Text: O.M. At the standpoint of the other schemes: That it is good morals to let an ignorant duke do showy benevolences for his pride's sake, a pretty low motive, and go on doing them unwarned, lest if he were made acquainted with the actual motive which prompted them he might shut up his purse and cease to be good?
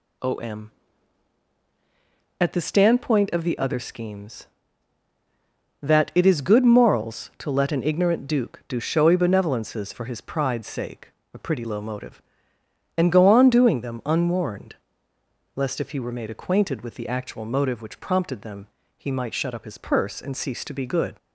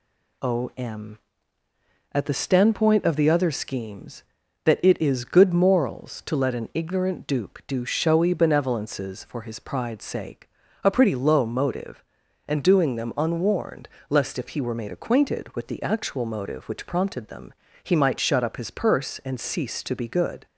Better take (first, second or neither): first